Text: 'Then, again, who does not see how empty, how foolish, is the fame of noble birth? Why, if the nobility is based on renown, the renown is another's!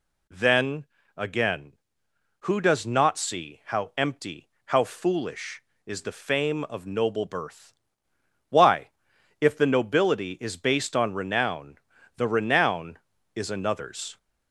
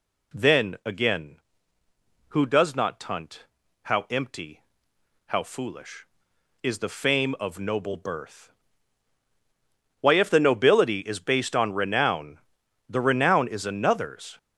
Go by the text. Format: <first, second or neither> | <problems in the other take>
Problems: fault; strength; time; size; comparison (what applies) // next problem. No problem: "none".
first | says "tunt" for "see"; at 2.9 s